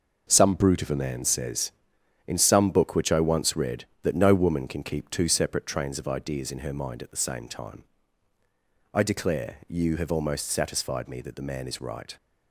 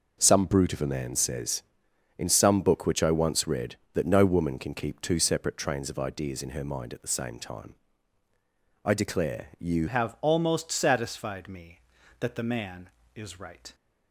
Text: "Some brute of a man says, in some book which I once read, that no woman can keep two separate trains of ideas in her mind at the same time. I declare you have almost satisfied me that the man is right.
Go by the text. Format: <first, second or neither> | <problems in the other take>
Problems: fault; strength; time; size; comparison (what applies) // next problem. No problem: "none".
first | changes voice at "have"; from 9.8 s on; 3.9 s long